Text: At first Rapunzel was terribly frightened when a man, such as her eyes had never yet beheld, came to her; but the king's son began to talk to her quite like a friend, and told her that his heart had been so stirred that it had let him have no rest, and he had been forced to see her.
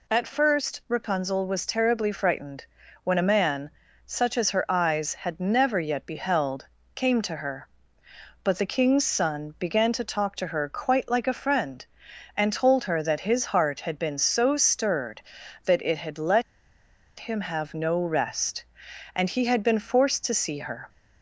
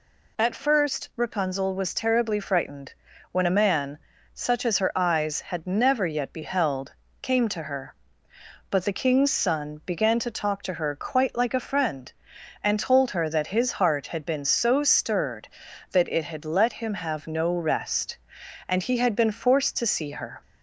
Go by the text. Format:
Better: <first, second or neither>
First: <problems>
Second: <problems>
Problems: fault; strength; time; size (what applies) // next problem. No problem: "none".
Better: second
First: pauses between "frightened" and "when"; at 2.6 s; 0.38 s long // pauses between "let" and "him"; noticeable; at 16.4 s; 0.75 s long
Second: pauses between "frightened" and "when"; at 2.9 s; 0.38 s long